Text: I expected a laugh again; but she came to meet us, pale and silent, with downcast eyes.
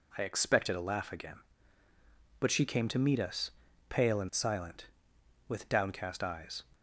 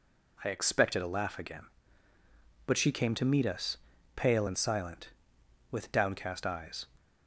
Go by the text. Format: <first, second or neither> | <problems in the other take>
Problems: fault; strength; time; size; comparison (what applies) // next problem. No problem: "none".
neither | none